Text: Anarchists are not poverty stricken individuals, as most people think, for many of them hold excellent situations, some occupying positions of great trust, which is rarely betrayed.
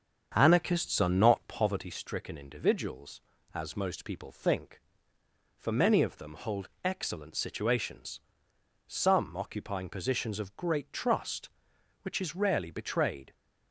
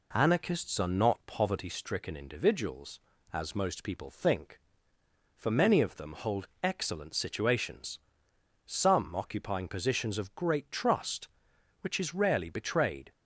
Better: second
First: starts louder than the rest; strong; until 1.7 s; 7.5 dB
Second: none

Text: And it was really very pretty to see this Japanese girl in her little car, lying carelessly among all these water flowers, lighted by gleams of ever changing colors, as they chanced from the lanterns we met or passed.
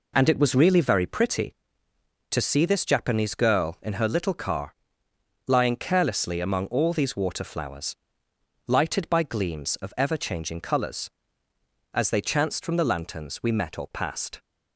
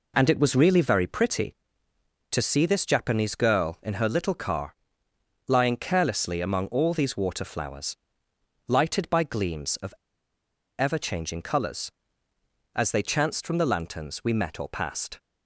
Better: first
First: none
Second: pauses between "of" and "ever"; noticeable; at 9.9 s; 0.84 s long

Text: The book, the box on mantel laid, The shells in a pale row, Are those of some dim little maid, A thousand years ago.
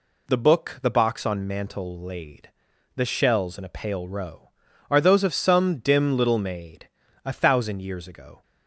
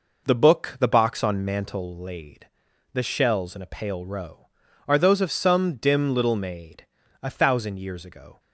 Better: first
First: none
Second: starts louder than the rest; noticeable; until 1.9 s; 5 dB

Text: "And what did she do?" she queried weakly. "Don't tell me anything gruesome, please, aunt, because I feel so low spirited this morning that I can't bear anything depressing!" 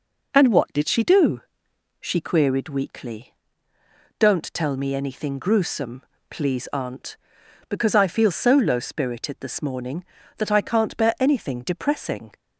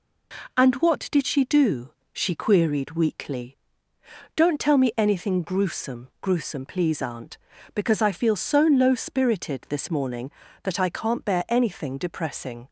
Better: first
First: none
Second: says "gruesome" twice; at 6.2 s

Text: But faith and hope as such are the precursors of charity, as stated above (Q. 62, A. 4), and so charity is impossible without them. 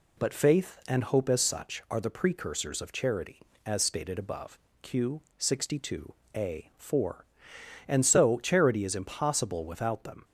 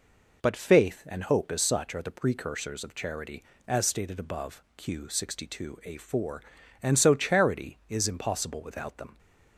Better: neither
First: none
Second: none

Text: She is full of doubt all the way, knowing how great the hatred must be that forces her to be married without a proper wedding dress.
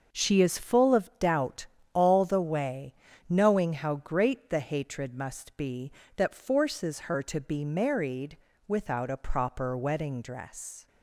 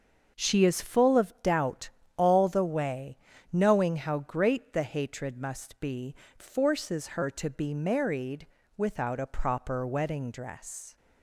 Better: first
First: starts louder than the rest; noticeable; until 1.2 s; 6 dB // pauses between "doubt" and "all"; slight; at 1.6 s; 0.26 s long // pauses between "married" and "without"; slight; at 8.3 s; 0.30 s long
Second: starts louder than the rest; until 1.4 s; 6.5 dB // pauses between "doubt" and "all"; slight; at 1.8 s; 0.26 s long // skips "that"; at 6.2 s // pauses between "married" and "without"; slight; at 8.4 s; 0.30 s long

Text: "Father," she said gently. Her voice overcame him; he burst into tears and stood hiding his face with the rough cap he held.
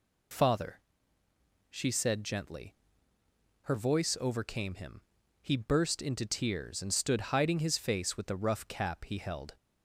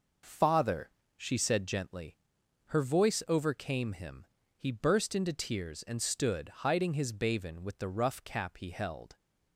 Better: first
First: none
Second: pauses between "stood" and "hiding"; slight; at 6.4 s; 0.18 s long // says "baven" for "face"; at 7.1 s

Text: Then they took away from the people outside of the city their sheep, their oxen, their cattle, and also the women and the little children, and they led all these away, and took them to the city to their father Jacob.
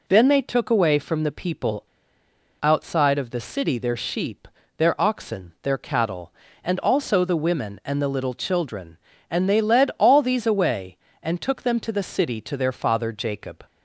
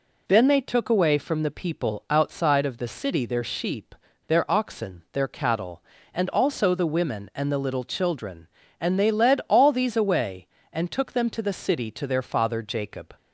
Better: second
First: pauses between "people" and "outside"; noticeable; at 1.8 s; 0.78 s long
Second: none

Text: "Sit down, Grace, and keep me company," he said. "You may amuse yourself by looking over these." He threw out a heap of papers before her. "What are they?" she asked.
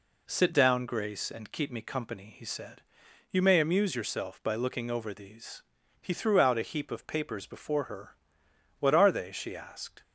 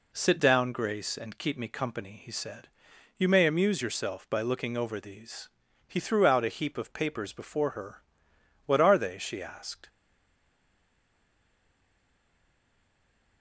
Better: first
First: none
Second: stays silent after the last word; strong; from 9.8 s on; 3.6 s long

